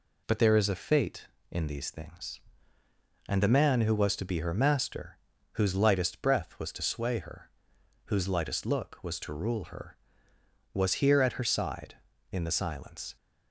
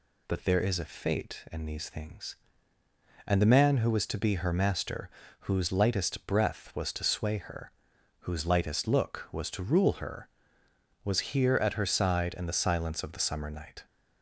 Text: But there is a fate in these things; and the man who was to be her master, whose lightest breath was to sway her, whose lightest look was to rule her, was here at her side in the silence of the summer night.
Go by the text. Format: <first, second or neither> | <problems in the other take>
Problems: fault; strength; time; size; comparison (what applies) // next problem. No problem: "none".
second | stops before "of the summer night"; at 13.1 s